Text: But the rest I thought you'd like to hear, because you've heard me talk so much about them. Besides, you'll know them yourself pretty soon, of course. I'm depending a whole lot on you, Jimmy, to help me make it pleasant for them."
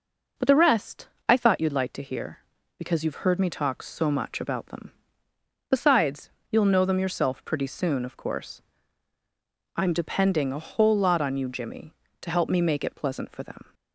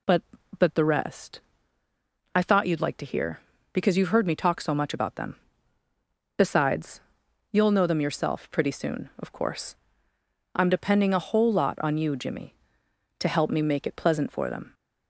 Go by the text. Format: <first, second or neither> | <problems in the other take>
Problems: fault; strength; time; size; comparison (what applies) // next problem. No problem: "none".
first | says "But" twice; at 0.5 s // pauses between "rest" and "I"; noticeable; at 1.3 s; 0.96 s long; slight in the first